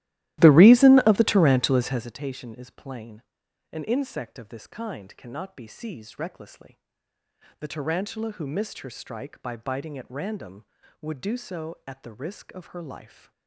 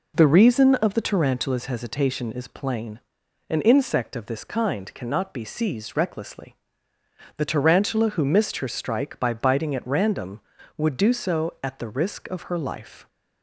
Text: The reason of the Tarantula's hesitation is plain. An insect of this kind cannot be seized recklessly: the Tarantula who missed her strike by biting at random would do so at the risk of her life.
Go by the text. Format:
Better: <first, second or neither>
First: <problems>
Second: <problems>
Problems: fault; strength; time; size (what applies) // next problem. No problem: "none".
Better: second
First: starts louder than the rest; strong; until 2.2 s; 15.5 dB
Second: none